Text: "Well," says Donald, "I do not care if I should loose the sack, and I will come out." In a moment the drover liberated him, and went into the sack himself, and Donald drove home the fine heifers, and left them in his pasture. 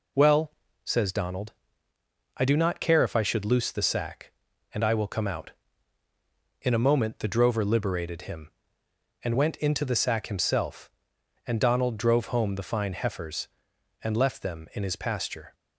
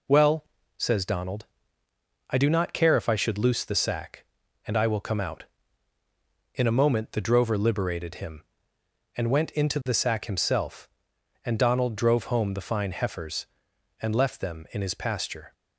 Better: neither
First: none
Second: none

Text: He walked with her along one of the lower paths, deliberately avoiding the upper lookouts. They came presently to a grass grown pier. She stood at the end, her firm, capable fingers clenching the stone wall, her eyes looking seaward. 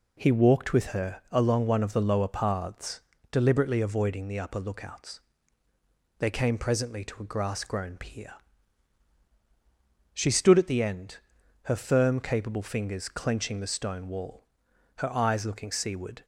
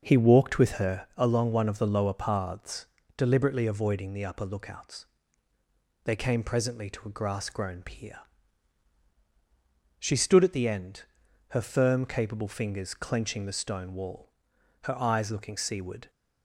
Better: first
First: none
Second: starts louder than the rest; noticeable; until 1.2 s; 6 dB

